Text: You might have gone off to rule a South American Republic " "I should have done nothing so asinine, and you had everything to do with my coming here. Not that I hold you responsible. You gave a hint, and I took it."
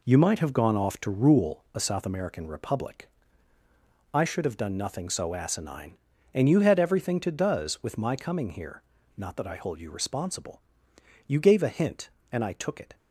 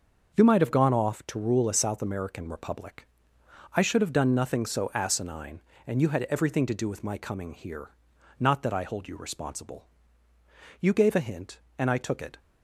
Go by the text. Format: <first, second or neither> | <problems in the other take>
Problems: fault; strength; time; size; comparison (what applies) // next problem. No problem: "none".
second | says "does" for "do"; at 7.2 s